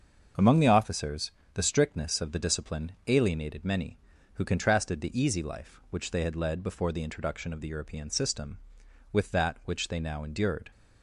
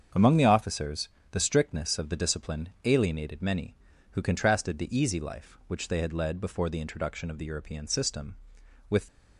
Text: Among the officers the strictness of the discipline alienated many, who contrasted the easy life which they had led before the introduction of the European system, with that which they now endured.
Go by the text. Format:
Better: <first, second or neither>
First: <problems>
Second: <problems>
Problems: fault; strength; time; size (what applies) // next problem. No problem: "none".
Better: first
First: starts louder than the rest; until 1.5 s; 6.5 dB // pauses between "officers" and "the"; slight; at 1.3 s; 0.22 s long // pauses between "discipline" and "alienated"; slight; at 2.9 s; 0.16 s long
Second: starts louder than the rest; until 1.3 s; 7 dB // pauses between "officers" and "the"; slight; at 1.0 s; 0.22 s long // pauses between "discipline" and "alienated"; slight; at 2.6 s; 0.16 s long // stops before "that which they now endured"; at 9.0 s